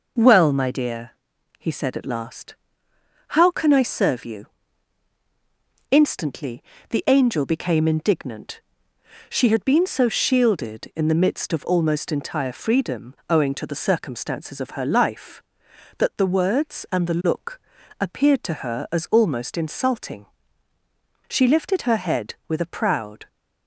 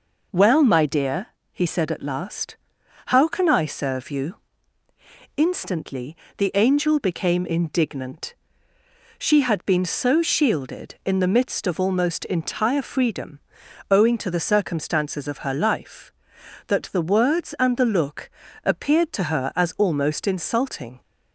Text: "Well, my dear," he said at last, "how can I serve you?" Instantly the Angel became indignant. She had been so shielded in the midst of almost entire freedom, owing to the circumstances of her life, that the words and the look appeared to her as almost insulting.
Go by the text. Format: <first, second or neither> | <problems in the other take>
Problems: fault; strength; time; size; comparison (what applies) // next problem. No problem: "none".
second | pauses between "Instantly" and "the"; slight; at 6.6 s; 0.26 s long; slight in the second // pauses between "look" and "appeared"; at 17.5 s; 0.40 s long; slight in the second // goes on to say "She lifted her head with a proud"; strong; from 21.2 s on; 1.9 s long